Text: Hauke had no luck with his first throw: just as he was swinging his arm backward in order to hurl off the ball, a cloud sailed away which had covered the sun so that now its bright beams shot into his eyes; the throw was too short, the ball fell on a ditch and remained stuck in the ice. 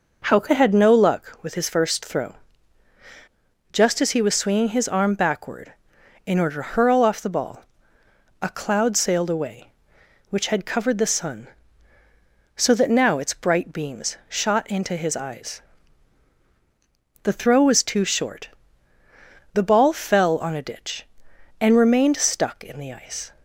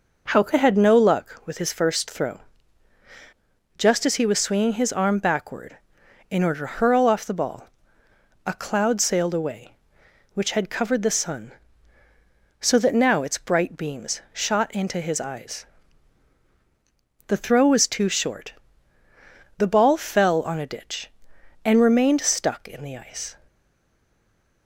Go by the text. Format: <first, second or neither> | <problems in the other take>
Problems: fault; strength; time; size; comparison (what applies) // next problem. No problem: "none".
first | stays silent after the last word; noticeable; from 23.4 s on; 1.2 s long